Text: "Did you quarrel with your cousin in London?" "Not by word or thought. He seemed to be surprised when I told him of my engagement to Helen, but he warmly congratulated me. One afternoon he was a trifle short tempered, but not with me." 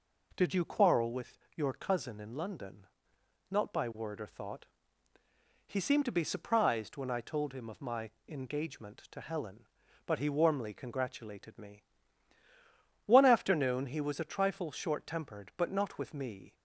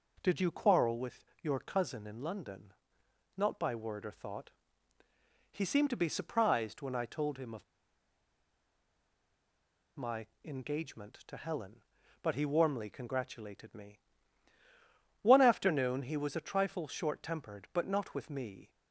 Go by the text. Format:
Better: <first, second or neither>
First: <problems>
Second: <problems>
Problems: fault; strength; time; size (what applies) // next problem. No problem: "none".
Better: first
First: pauses between "with" and "your"; slight; at 1.3 s; 0.18 s long // pauses between "my" and "engagement"; slight; at 8.0 s; 0.18 s long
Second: pauses between "with" and "your"; slight; at 1.2 s; 0.18 s long // pauses between "of" and "my"; strong; at 7.6 s; 2.3 s long // pauses between "my" and "engagement"; slight; at 10.2 s; 0.18 s long